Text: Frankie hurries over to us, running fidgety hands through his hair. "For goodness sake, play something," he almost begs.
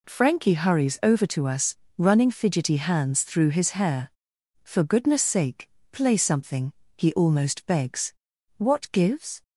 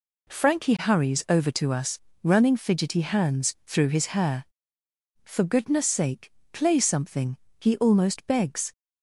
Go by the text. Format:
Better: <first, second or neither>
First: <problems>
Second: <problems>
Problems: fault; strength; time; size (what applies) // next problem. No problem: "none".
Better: second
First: goes on to say "What gives"; noticeable; from 8.5 s on; 0.84 s long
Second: none